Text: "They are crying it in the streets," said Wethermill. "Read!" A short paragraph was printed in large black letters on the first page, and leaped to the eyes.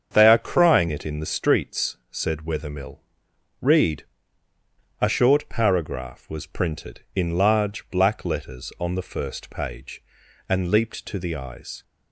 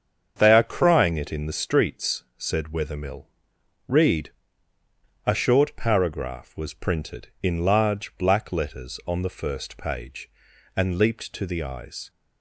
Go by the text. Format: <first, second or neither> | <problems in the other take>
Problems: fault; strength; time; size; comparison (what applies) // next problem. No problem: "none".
neither | starts louder than the rest; strong; the same in both